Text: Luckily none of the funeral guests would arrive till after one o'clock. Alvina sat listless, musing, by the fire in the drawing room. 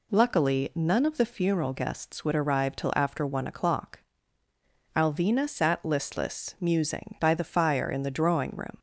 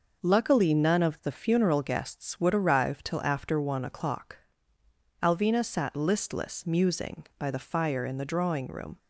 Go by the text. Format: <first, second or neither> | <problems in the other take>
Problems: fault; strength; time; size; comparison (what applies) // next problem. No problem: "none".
neither | none